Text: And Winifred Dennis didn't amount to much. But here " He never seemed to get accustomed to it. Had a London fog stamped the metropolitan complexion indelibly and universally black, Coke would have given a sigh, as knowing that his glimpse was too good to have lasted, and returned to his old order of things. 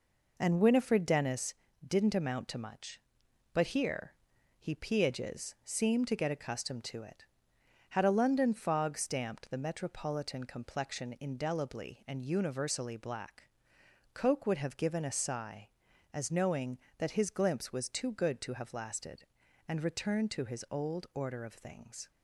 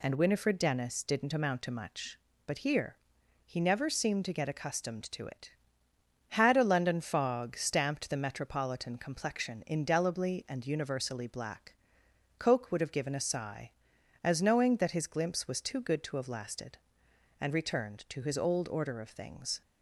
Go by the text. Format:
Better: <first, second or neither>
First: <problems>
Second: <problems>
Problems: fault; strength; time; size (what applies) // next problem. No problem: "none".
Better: second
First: pauses between "Dennis" and "didn't"; slight; at 1.5 s; 0.32 s long // says "peages" for "never"; at 4.7 s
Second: none